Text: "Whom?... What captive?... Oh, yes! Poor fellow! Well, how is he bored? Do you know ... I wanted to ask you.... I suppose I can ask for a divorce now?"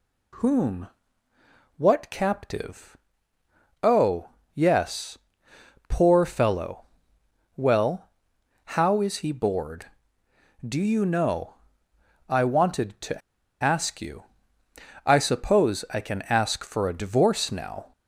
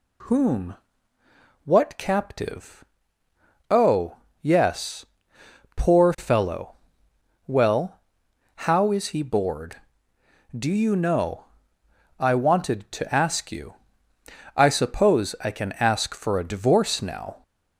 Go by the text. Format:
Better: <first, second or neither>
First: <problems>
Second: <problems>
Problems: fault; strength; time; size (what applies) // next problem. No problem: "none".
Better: second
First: pauses between "to" and "ask"; at 13.2 s; 0.43 s long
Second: none